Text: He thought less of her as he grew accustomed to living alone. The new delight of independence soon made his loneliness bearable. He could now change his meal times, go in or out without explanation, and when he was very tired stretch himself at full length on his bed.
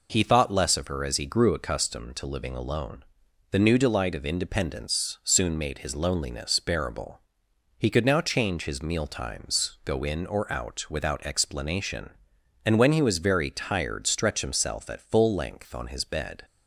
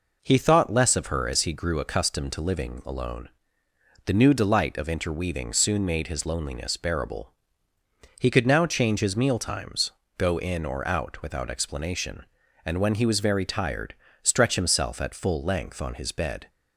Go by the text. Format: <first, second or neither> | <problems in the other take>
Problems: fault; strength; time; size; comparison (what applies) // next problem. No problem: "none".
first | says "interweaving" for "independence"; at 4.8 s // pauses between "tired" and "stretch"; slight; at 13.9 s; 0.28 s long